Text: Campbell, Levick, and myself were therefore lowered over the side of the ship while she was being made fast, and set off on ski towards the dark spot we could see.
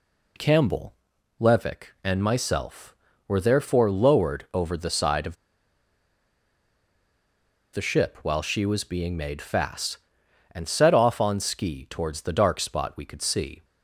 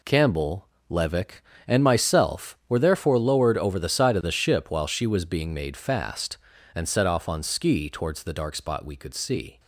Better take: second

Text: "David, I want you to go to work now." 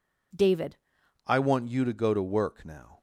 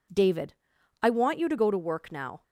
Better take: second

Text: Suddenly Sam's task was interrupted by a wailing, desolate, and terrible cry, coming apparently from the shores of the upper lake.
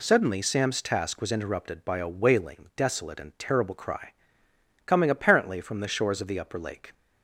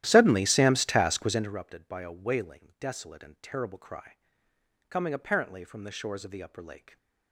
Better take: first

